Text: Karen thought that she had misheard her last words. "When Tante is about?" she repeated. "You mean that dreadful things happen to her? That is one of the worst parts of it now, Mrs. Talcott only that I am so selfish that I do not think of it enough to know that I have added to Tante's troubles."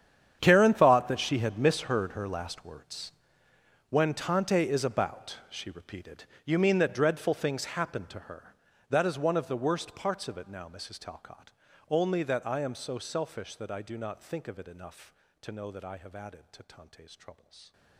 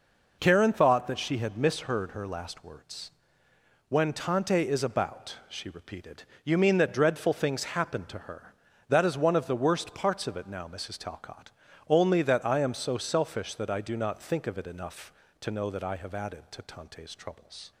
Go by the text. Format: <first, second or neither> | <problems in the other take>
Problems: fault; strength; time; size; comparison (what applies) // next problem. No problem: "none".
second | gets quieter; strong; throughout; 18 dB // pauses between "Talcott" and "only"; at 11.5 s; 0.40 s long; also in the second